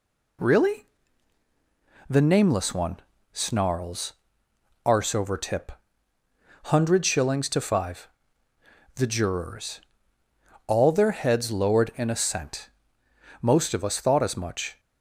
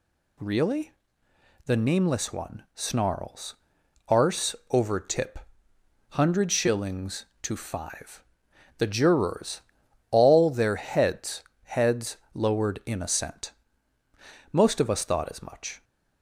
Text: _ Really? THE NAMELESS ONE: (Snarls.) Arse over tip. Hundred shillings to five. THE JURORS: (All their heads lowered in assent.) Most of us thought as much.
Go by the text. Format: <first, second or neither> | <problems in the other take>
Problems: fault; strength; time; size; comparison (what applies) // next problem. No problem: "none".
first | pauses between "Arse" and "over"; slight; at 4.5 s; 0.16 s long // says "heads" twice; at 11.6 s